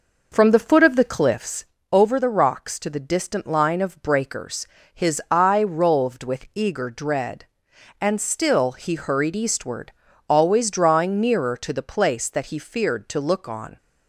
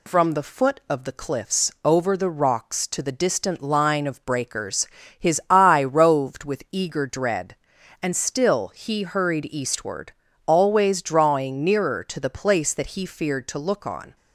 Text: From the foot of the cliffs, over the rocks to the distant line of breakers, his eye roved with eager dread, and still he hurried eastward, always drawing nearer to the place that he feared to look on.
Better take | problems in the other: second | starts louder than the rest; noticeable; until 1.5 s; 5.5 dB

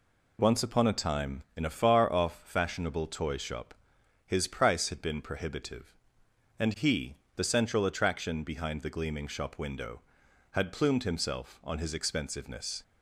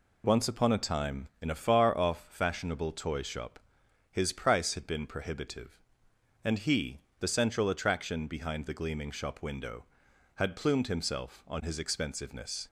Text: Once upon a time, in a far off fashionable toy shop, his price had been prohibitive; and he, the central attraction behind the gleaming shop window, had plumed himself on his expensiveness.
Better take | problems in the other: neither | none

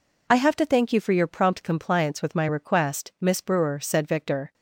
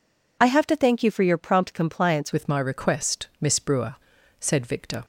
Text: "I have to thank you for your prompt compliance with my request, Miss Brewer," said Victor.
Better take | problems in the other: first | changes voice at "with"; from 2.3 s on; 2.7 s long

